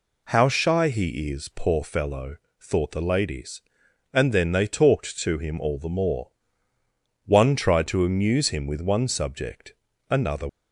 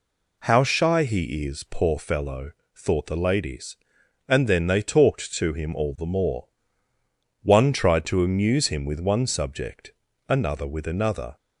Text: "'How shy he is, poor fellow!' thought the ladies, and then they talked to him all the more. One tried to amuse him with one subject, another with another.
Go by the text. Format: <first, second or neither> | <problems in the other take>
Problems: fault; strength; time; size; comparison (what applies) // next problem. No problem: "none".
second | stops before "with another"; at 10.4 s